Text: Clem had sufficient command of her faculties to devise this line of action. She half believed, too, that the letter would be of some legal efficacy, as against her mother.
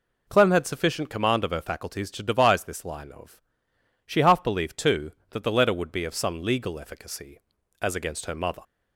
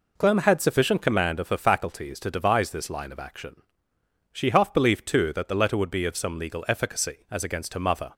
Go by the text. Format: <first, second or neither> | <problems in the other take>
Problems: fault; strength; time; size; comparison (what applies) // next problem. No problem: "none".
second | skips "action"; at 3.7 s